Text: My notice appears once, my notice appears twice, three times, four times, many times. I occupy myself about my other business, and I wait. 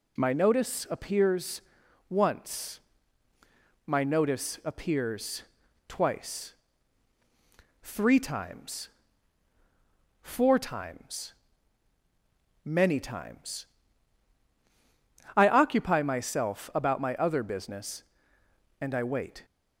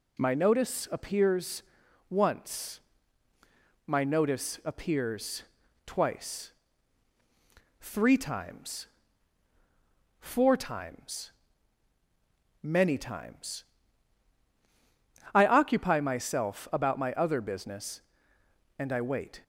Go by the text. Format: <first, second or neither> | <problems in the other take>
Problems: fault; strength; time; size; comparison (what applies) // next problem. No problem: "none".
neither | pauses between "appears" and "once"; noticeable; the same in both // pauses between "appears" and "twice"; the same in both